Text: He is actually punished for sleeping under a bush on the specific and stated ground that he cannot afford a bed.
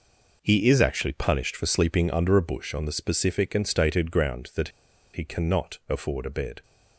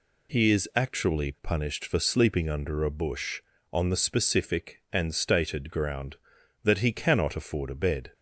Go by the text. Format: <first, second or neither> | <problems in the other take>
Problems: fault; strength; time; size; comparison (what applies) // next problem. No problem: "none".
second | pauses between "that" and "he"; at 4.6 s; 0.44 s long